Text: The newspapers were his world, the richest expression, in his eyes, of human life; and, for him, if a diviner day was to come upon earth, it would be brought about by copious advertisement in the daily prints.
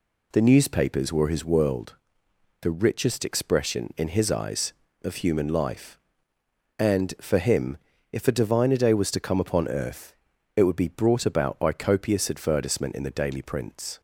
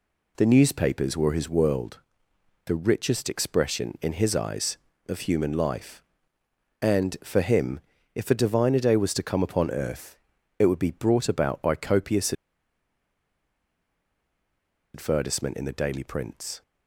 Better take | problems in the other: first | pauses between "copious" and "advertisement"; strong; at 12.3 s; 2.6 s long

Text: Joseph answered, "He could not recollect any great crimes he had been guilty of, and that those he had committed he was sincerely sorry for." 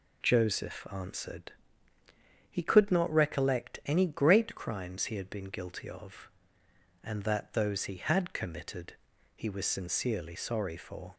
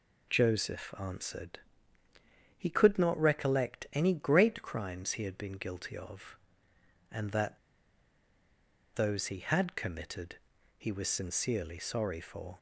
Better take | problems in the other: first | pauses between "that" and "those"; strong; at 7.5 s; 1.3 s long // pauses between "committed" and "he"; at 10.3 s; 0.42 s long; also in the first

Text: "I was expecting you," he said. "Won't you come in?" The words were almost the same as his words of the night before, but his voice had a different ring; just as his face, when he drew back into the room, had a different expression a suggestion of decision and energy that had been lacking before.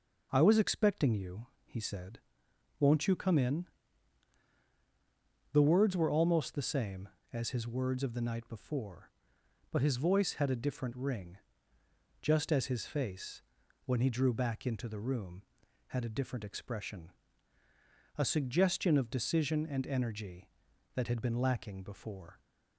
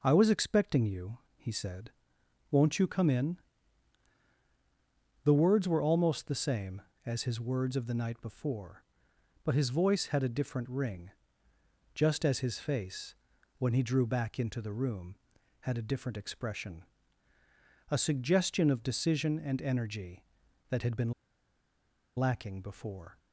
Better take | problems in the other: first | pauses between "expression" and "a"; at 16.8 s; 1.0 s long; also in the first // pauses between "been" and "lacking"; at 21.1 s; 1.0 s long

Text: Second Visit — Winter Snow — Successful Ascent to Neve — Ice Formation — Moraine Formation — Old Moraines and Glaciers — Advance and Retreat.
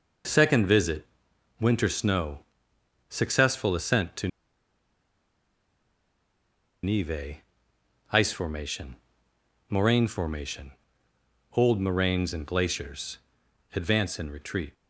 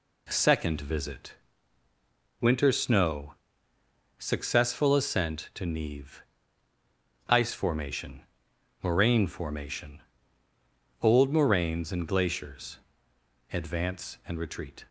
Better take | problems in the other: second | pauses between "to" and "Neve"; strong; at 4.2 s; 2.5 s long

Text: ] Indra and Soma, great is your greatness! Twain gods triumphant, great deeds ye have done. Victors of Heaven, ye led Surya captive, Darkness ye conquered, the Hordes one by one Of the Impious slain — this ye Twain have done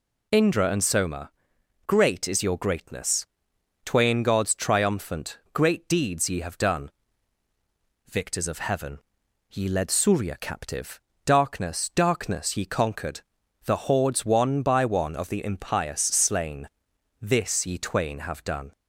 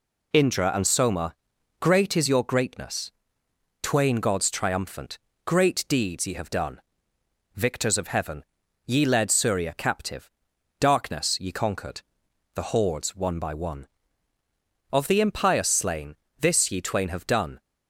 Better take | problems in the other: second | says "Darkness" twice; at 11.9 s

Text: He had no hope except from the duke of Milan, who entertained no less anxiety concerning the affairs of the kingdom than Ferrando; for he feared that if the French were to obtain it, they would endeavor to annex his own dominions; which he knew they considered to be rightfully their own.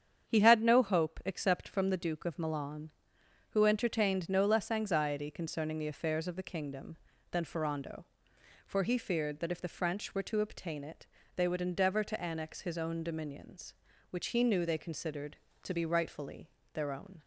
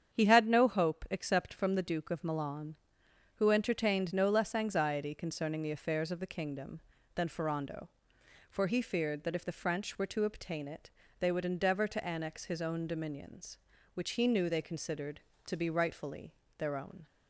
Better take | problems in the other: neither | starts louder than the rest; strong; the same in both // pauses between "rightfully" and "their"; slight; the same in both

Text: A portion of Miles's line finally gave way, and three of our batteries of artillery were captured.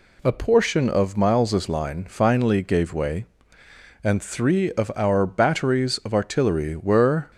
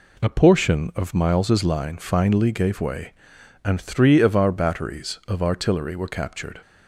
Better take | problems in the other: second | stops before "captured"; at 7.3 s

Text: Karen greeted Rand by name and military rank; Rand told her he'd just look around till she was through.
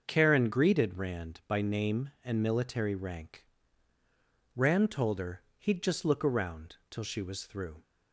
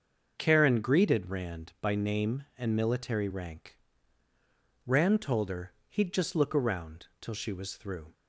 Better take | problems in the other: neither | starts louder than the rest; the same in both // pauses between "her" and "he'd"; slight; the same in both // pauses between "around" and "till"; slight; the same in both

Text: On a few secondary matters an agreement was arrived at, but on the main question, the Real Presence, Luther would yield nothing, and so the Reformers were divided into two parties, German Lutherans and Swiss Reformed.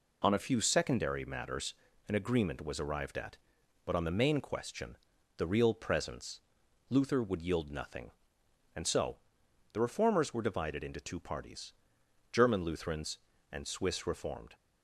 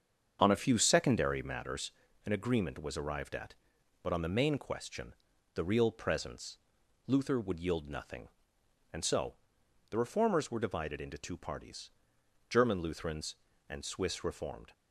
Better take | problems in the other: first | starts louder than the rest; strong; until 1.7 s; 7 dB // pauses between "matters" and "an"; slight; at 1.9 s; 0.34 s long; slight in the first // pauses between "so" and "the"; noticeable; at 9.3 s; 0.56 s long; noticeable in the first

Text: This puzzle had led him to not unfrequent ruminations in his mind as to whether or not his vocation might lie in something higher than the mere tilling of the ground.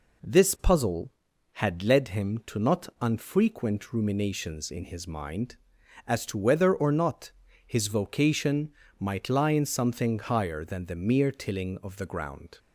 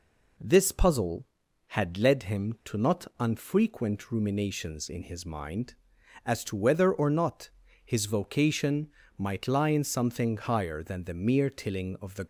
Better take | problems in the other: first | pauses between "not" and "his"; slight; at 7.5 s; 0.34 s long; slight in the first // pauses between "vocation" and "might"; slight; at 8.9 s; 0.26 s long; slight in the first // stops before "ground"; at 12.2 s

